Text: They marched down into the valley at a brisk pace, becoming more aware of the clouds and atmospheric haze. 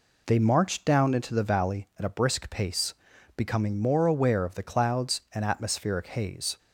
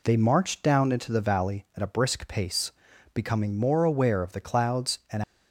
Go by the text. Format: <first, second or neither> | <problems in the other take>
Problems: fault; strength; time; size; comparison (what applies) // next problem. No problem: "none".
first | stops before "atmospheric haze"; at 5.2 s